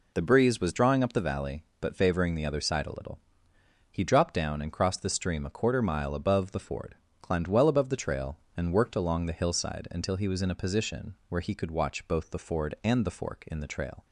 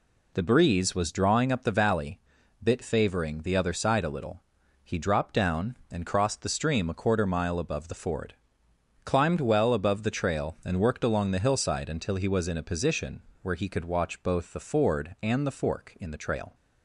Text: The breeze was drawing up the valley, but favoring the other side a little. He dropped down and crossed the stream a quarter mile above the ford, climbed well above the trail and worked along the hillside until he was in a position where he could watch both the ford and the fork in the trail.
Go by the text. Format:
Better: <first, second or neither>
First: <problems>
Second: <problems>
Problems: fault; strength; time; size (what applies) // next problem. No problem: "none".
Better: first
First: none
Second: says "bit" for "but"; at 2.6 s // pauses between "position" and "where"; slight; at 13.2 s; 0.22 s long